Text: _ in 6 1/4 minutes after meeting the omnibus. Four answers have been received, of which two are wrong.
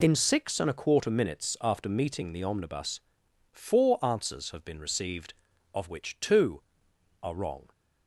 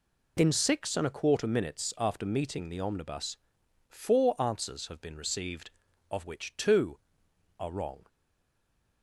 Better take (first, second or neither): first